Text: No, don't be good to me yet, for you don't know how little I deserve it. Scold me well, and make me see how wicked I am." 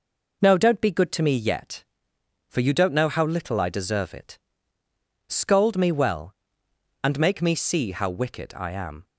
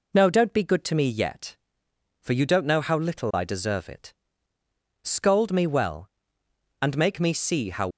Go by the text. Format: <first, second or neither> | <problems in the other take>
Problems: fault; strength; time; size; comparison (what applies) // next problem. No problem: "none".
first | stops before "wicked I am"; at 7.9 s